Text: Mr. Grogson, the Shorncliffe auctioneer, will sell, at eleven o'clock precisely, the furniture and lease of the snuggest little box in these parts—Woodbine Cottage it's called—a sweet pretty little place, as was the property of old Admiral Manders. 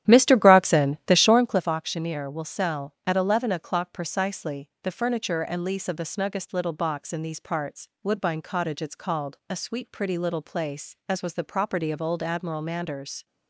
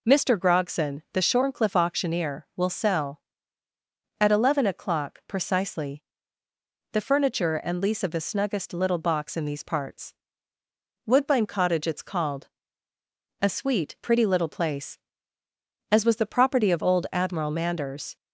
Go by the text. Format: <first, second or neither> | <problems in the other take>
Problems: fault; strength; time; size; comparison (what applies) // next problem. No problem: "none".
second | starts louder than the rest; strong; until 1.7 s; 11.5 dB